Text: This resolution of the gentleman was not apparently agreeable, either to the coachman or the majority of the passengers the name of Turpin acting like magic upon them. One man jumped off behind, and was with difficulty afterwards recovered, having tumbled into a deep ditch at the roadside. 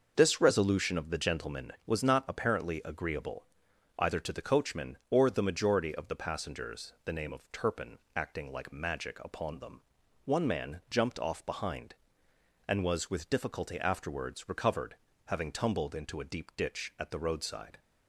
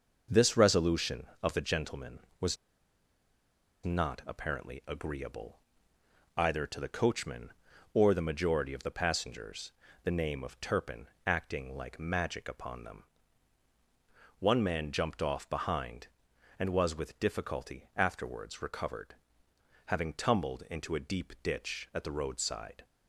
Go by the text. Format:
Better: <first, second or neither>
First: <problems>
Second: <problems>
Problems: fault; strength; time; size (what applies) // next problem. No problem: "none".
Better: first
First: starts louder than the rest; noticeable; until 1.1 s; 6 dB // pauses between "Turpin" and "acting"; slight; at 7.9 s; 0.18 s long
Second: starts louder than the rest; until 1.4 s; 6 dB // pauses between "was" and "not"; strong; at 2.5 s; 1.2 s long // pauses between "passengers" and "the"; slight; at 9.7 s; 0.30 s long // pauses between "Turpin" and "acting"; slight; at 11.0 s; 0.18 s long